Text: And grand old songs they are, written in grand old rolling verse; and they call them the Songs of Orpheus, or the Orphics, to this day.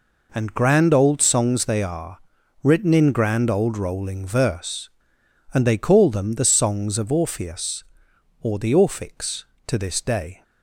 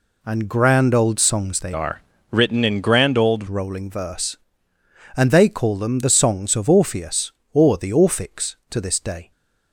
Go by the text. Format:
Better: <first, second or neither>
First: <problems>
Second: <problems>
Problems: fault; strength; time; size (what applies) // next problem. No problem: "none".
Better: first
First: none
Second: changes voice from "are" to "old"; from 1.7 to 3.4 s; 1.7 s long